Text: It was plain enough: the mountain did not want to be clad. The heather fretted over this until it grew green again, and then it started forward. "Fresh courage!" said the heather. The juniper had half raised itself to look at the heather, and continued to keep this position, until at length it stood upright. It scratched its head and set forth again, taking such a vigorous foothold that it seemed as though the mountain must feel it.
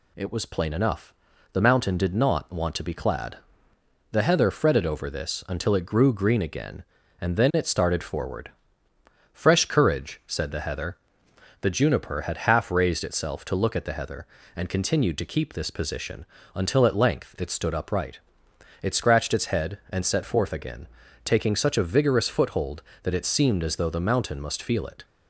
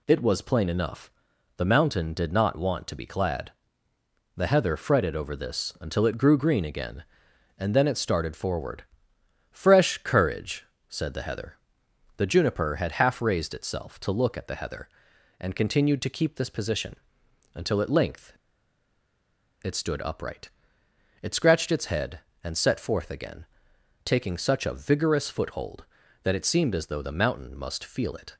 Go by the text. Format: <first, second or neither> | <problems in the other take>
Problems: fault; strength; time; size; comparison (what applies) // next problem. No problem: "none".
first | pauses between "length" and "it"; strong; at 18.3 s; 1.3 s long